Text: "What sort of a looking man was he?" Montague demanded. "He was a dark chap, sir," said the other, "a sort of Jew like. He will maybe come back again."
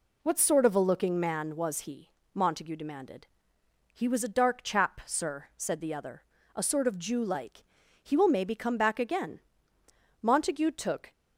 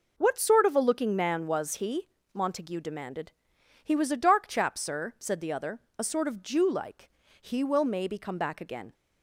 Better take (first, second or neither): second